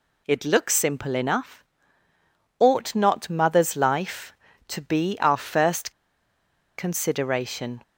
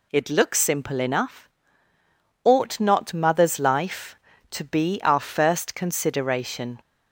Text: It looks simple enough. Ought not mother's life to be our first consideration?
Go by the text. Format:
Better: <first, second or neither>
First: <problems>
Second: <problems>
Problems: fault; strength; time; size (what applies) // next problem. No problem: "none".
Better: second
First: pauses between "first" and "consideration"; noticeable; at 5.8 s; 0.87 s long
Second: none